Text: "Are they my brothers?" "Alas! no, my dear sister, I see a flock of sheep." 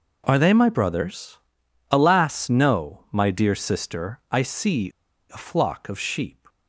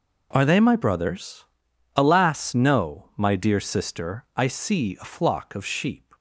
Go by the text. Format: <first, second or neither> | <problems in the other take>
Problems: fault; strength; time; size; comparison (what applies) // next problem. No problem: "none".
second | pauses between "see" and "a"; at 4.9 s; 0.41 s long